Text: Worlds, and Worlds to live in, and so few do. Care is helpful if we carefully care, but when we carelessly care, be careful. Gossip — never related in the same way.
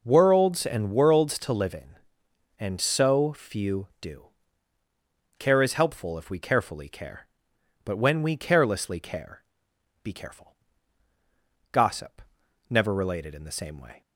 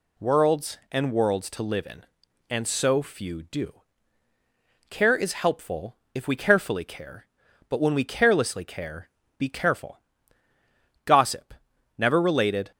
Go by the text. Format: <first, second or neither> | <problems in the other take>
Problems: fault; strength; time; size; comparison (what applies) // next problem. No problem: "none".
first | pauses between "helpful" and "if"; slight; at 5.9 s; 0.20 s long // stops before "in the same way"; at 12.7 s